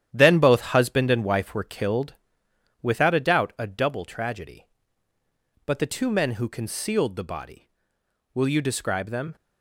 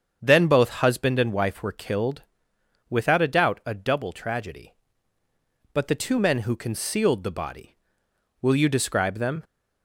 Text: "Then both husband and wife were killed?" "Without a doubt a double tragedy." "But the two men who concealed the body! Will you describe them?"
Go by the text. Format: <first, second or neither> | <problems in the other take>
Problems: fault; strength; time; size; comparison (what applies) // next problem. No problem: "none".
second | gets quieter; strong; throughout; 8.5 dB // starts louder than the rest; strong; until 1.1 s; 10.5 dB; strong in the second